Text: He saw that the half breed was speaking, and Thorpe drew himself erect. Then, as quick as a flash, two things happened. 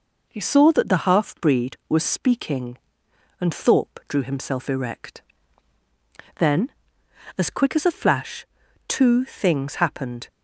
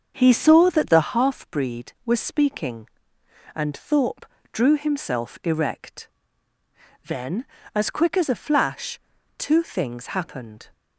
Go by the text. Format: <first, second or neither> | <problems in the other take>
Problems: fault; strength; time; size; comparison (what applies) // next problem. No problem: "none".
first | starts louder than the rest; until 1.2 s; 7 dB // pauses between "Thorpe" and "drew"; slight; at 4.2 s; 0.28 s long